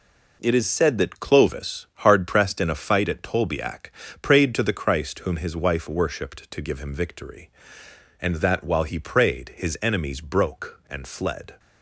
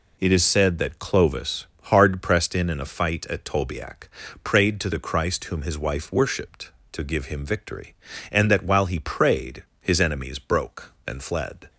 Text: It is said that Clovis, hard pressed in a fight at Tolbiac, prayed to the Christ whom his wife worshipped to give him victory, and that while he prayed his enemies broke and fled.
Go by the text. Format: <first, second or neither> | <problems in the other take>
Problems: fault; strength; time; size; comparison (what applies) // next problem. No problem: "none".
first | says "in" twice; at 2.6 s // pauses between "prayed" and "his"; slight; at 9.6 s; 0.16 s long